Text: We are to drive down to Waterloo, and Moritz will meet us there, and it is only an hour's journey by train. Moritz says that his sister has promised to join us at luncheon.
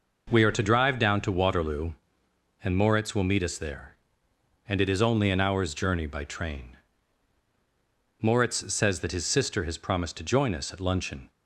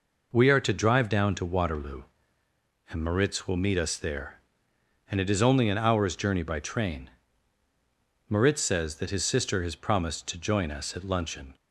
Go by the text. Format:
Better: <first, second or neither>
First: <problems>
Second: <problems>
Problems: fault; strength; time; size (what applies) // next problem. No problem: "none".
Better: neither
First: none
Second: none